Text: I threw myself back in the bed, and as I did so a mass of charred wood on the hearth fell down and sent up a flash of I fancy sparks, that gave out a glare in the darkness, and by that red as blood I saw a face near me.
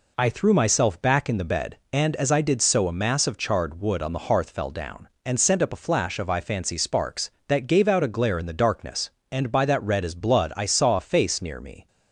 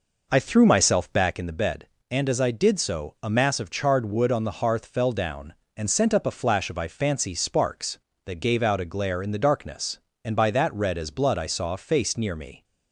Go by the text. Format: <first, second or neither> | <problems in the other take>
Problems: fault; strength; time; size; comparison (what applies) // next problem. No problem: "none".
first | starts louder than the rest; noticeable; until 1.5 s; 5 dB